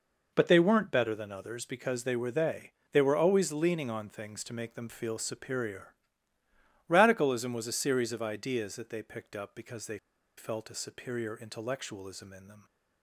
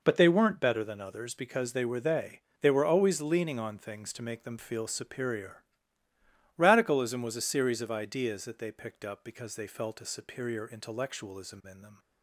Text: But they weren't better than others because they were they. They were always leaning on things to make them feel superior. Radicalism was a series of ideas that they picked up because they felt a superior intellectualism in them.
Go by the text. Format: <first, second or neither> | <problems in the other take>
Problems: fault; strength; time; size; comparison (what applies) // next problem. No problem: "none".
second | pauses between "they" and "felt"; at 9.9 s; 0.40 s long